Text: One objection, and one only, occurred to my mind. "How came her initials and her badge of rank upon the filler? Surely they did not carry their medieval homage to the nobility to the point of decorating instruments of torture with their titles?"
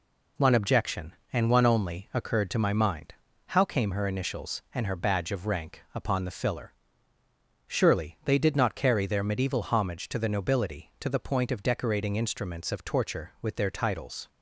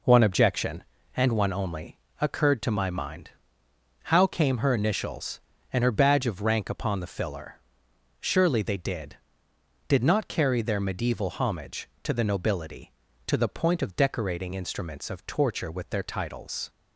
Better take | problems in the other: first | says "did" twice; at 9.8 s

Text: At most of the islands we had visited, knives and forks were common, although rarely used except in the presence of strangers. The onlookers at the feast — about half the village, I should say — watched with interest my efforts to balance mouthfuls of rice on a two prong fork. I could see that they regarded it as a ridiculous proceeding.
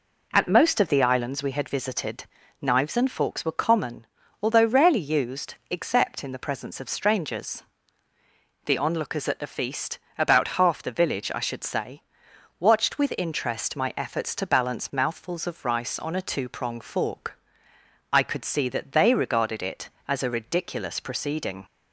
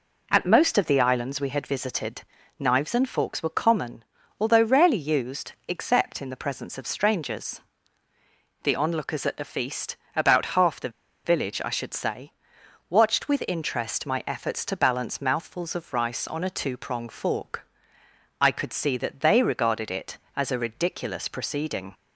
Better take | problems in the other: first | pauses between "the" and "village"; slight; at 10.8 s; 0.35 s long

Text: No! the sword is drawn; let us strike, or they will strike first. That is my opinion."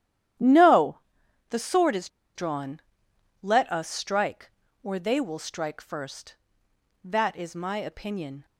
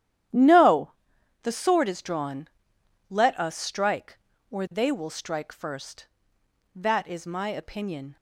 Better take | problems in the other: second | starts louder than the rest; strong; until 1.9 s; 11.5 dB; strong in the second // pauses between "is" and "drawn"; slight; at 2.0 s; 0.27 s long

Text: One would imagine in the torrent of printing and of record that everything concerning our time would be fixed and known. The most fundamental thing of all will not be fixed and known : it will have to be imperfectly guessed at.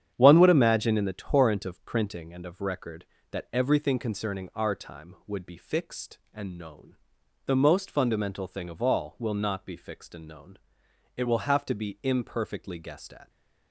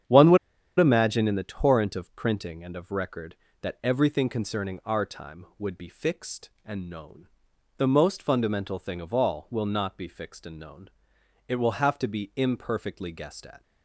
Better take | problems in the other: first | starts louder than the rest; strong; until 1.5 s; 8.5 dB; strong in the first // pauses between "would" and "imagine"; at 0.3 s; 0.42 s long

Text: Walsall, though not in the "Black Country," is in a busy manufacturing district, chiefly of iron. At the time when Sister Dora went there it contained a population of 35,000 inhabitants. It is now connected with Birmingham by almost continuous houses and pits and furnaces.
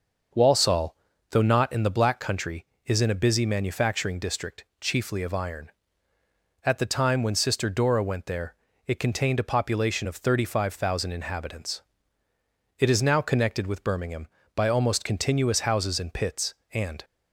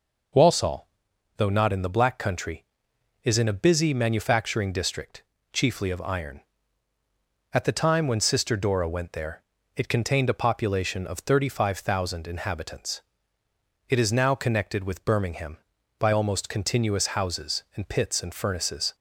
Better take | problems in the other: second | starts louder than the rest; until 1.6 s; 6.5 dB // pauses between "there" and "it"; slight; at 8.5 s; 0.32 s long; slight in the second // stops before "furnaces"; at 17.0 s

